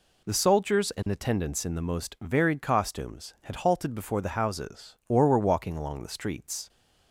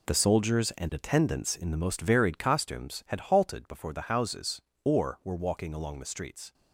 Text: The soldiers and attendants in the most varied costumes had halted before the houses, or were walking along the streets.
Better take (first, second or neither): first